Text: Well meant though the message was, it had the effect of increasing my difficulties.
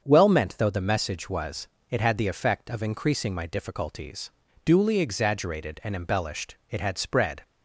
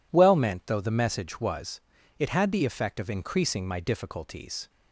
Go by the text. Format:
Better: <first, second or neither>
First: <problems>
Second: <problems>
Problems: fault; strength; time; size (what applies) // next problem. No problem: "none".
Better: second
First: starts louder than the rest; until 1.0 s; 7 dB // goes on to say "Duly exaggerated and embellished it had spread"; strong; from 4.6 s on; 2.7 s long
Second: none